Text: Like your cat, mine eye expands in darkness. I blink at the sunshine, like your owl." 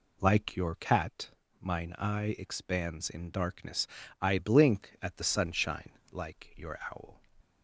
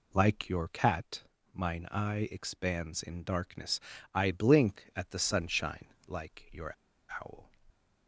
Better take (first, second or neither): first